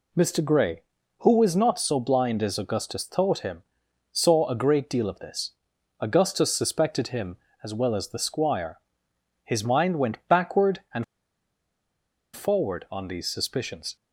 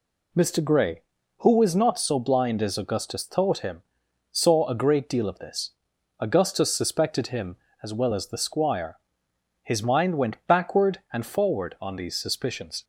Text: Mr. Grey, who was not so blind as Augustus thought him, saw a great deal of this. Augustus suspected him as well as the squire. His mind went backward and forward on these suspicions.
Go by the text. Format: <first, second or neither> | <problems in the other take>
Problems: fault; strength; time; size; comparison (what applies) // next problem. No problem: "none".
second | pauses between "and" and "forward"; strong; at 11.0 s; 1.3 s long